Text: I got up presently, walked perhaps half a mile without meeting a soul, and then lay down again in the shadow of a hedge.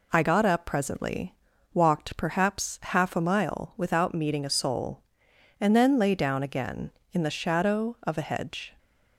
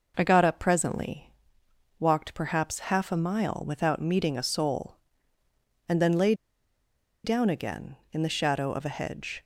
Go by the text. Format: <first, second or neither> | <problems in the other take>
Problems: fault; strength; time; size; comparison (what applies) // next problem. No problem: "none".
first | pauses between "lay" and "down"; noticeable; at 6.3 s; 0.91 s long